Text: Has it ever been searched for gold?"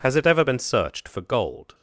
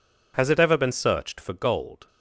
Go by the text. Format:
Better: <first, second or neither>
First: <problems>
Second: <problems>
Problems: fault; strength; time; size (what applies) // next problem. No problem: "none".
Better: neither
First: none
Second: none